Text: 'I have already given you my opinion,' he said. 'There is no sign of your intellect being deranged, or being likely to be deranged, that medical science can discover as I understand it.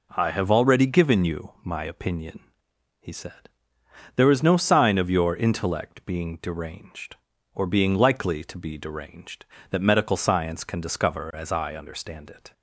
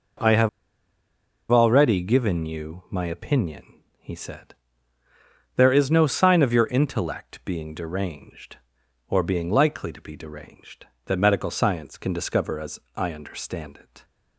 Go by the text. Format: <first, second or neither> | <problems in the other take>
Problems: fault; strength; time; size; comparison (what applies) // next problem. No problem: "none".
first | pauses between "have" and "already"; at 0.4 s; 1.0 s long // pauses between "as" and "I"; slight; at 12.7 s; 0.16 s long